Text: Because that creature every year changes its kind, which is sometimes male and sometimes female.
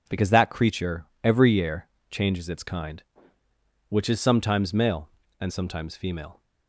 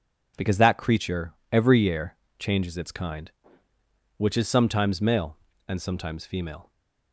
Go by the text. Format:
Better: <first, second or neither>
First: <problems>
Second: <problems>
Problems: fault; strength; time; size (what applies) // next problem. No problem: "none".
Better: neither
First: pauses between "creature" and "every"; slight; at 1.0 s; 0.17 s long // pauses between "year" and "changes"; slight; at 1.8 s; 0.22 s long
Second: pauses between "creature" and "every"; slight; at 1.3 s; 0.18 s long // pauses between "year" and "changes"; slight; at 2.1 s; 0.22 s long